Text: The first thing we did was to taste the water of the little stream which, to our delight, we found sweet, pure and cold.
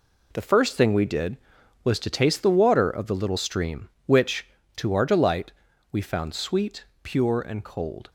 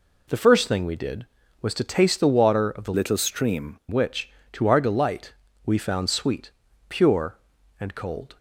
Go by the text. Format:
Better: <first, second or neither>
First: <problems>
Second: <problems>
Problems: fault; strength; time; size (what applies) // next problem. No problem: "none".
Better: first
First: none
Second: changes voice from "little" to "stream"; from 2.9 to 3.7 s; 0.8 s long